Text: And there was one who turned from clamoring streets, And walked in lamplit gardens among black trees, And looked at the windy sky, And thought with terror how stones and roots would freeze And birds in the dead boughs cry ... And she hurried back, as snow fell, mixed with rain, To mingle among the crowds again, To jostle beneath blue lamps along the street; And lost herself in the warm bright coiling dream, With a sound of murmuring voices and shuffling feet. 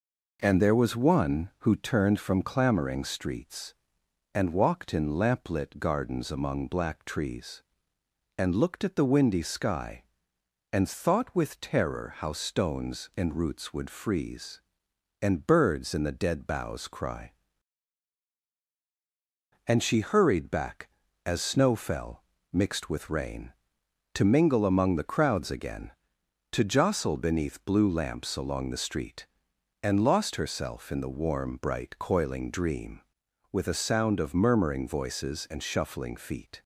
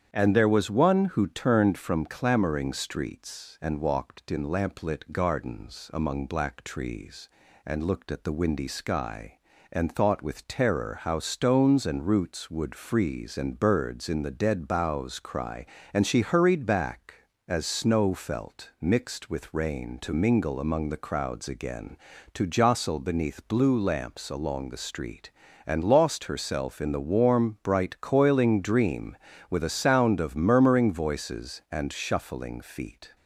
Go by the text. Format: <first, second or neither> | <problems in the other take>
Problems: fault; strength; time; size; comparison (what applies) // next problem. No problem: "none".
first | starts louder than the rest; strong; until 1.1 s; 9 dB // says "felt" for "fell"; at 18.1 s